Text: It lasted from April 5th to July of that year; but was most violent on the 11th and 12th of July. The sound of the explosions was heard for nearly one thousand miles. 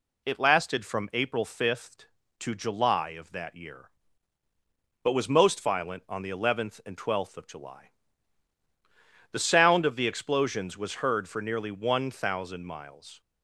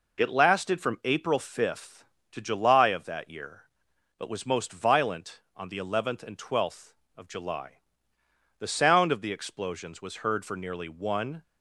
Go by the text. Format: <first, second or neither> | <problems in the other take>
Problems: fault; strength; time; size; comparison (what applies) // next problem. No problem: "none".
first | stops before "thousand miles"; at 11.4 s